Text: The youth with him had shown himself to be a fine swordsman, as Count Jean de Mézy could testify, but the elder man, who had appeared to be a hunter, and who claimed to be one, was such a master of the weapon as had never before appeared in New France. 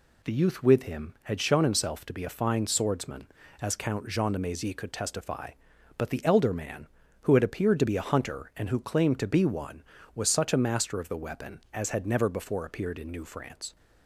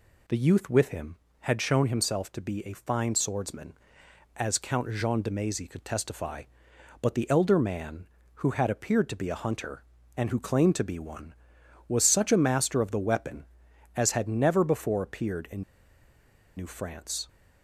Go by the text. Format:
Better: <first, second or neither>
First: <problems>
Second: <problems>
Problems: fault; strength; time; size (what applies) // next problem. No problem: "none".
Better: first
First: none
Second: pauses between "in" and "New"; noticeable; at 15.6 s; 0.94 s long